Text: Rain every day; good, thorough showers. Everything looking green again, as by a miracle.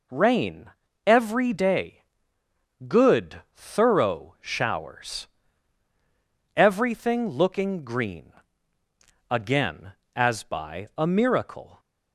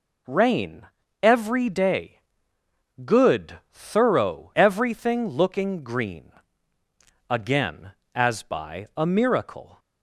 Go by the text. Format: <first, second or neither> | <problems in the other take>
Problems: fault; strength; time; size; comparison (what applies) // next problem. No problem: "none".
first | pauses between "Rain" and "every"; slight; at 0.8 s; 0.34 s long; slight in the first // skips "showers"; at 4.5 s // pauses between "green" and "again"; at 6.3 s; 1.0 s long; also in the first